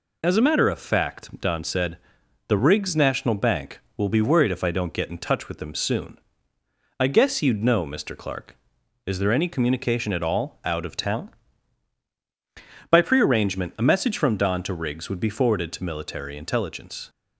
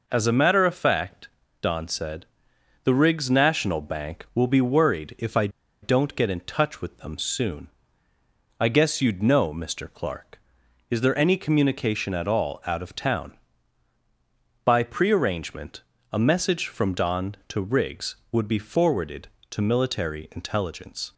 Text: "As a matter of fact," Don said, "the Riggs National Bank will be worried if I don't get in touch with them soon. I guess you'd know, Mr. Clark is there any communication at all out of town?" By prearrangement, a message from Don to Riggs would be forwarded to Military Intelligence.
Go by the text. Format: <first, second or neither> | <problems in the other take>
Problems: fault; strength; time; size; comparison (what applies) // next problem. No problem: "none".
first | pauses between "I" and "don't"; slight; at 5.4 s; 0.34 s long